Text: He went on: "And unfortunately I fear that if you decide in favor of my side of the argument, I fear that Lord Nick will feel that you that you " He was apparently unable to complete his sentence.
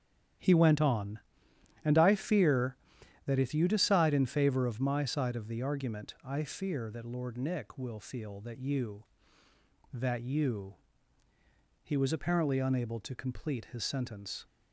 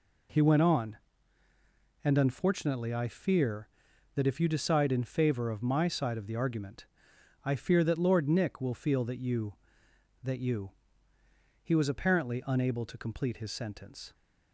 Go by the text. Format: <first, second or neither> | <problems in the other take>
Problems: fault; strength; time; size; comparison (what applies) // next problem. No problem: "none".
second | starts louder than the rest; strong; until 2.0 s; 10 dB // skips "unfortunately"; at 1.9 s